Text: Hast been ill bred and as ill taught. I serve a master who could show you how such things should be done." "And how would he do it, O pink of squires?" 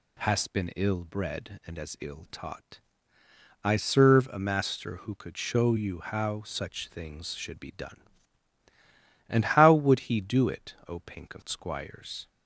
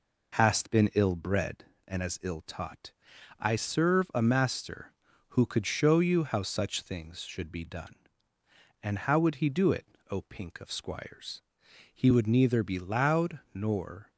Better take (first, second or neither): first